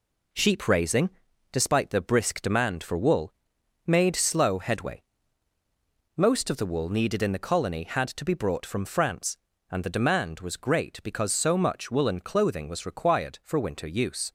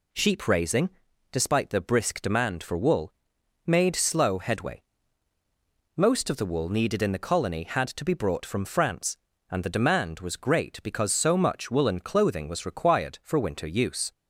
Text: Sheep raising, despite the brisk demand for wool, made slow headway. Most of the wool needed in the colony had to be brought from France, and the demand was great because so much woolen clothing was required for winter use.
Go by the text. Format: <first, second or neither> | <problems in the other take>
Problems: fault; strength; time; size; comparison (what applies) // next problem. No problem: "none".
second | gets quieter; noticeable; throughout; 4.5 dB